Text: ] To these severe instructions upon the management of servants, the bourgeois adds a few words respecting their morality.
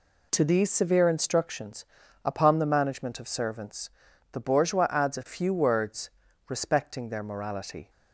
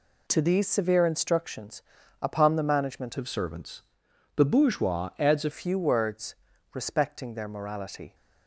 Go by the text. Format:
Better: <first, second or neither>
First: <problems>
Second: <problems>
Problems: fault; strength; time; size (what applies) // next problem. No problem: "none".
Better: first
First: pauses between "instructions" and "upon"; at 1.8 s; 0.38 s long // pauses between "words" and "respecting"; at 6.0 s; 0.38 s long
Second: pauses between "instructions" and "upon"; at 1.8 s; 0.38 s long // changes voice from "of" to "a"; from 3.1 to 5.4 s; 2.3 s long // pauses between "words" and "respecting"; at 6.3 s; 0.38 s long